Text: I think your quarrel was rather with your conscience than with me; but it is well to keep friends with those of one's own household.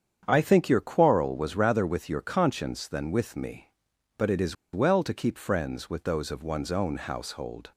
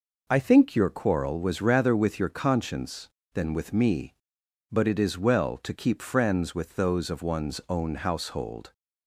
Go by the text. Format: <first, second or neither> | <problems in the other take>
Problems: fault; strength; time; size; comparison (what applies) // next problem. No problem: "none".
second | starts louder than the rest; strong; until 1.2 s; 8 dB // pauses between "is" and "well"; slight; at 4.5 s; 0.18 s long